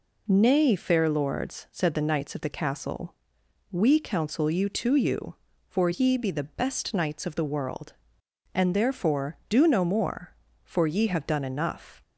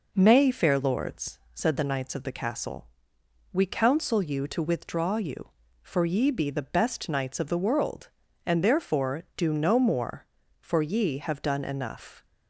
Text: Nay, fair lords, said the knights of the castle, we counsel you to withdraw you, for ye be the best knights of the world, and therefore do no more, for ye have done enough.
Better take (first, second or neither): second